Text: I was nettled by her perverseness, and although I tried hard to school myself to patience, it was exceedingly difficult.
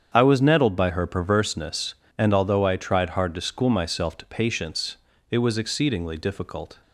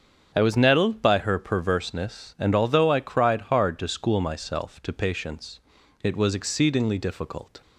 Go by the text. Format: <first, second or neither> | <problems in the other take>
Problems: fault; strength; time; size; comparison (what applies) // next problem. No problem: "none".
first | starts louder than the rest; strong; until 1.3 s; 7.5 dB; strong in the first // says "cried" for "tried"; at 3.0 s